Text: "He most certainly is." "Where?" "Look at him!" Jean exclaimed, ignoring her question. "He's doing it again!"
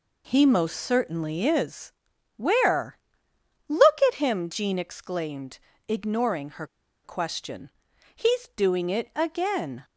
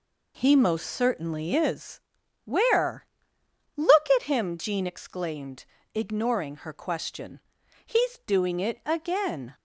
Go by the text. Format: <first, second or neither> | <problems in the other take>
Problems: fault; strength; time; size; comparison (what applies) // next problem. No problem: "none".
second | pauses between "her" and "question"; at 6.6 s; 0.39 s long